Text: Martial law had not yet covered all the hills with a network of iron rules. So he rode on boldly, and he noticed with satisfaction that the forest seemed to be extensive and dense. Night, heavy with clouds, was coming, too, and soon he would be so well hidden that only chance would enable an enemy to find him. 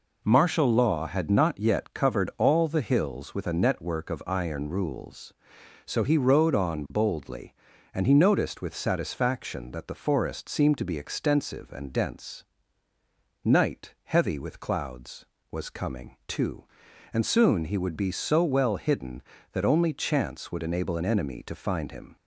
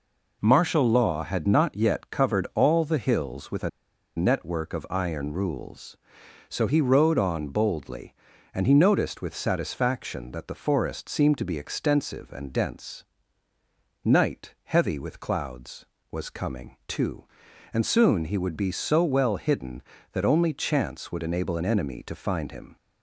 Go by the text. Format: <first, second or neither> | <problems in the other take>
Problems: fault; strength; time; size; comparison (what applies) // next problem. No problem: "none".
first | pauses between "a" and "network"; noticeable; at 3.6 s; 0.47 s long